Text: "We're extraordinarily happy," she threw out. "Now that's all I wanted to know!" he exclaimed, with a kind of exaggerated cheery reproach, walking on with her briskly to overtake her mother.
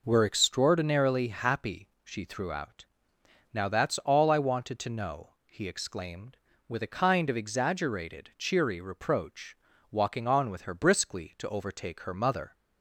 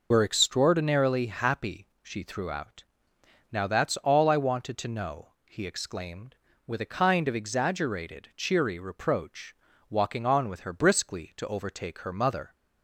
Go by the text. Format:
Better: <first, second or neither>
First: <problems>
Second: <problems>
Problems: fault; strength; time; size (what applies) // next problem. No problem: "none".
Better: first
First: none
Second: loses the start of "We're"; at 0.1 s; 75 ms